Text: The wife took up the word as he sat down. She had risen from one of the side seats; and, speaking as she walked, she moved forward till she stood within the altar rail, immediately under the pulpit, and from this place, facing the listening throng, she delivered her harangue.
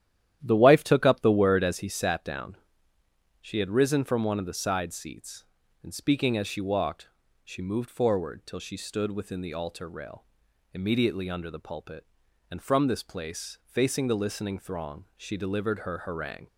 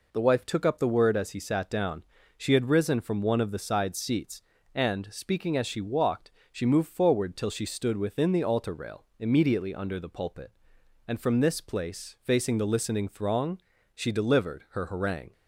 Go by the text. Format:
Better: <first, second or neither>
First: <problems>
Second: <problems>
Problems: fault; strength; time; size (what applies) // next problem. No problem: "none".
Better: second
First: starts louder than the rest; strong; until 1.9 s; 11.5 dB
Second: none